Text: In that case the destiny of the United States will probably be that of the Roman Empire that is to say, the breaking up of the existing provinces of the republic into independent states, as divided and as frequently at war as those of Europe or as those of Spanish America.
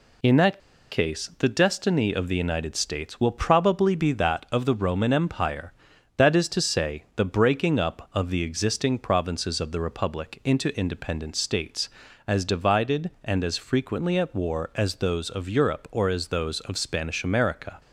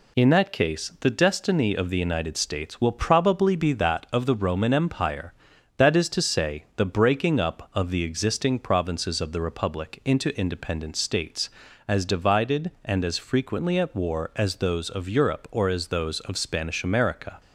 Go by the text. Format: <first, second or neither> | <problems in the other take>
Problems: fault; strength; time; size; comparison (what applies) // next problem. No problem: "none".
second | pauses between "that" and "case"; slight; at 0.5 s; 0.32 s long